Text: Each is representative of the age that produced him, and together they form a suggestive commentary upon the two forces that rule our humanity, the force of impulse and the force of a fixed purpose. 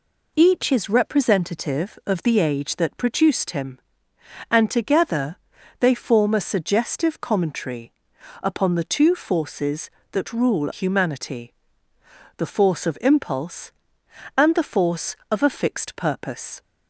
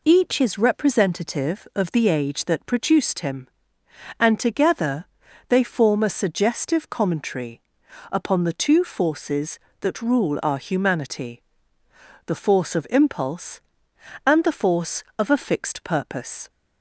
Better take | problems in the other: second | pauses between "together" and "they"; at 5.3 s; 0.42 s long; also in the second // pauses between "commentary" and "upon"; noticeable; at 7.9 s; 0.50 s long; noticeable in the second // skips "our"; at 10.7 s

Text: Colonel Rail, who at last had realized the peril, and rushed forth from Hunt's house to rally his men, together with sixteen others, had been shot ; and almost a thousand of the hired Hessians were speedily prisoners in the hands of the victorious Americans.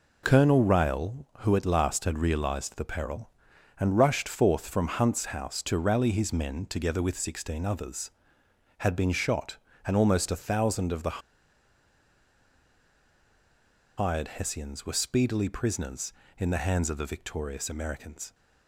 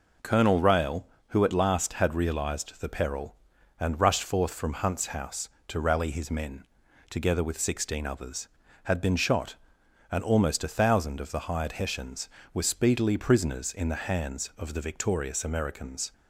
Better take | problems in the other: second | pauses between "the" and "hired"; strong; at 11.2 s; 2.7 s long

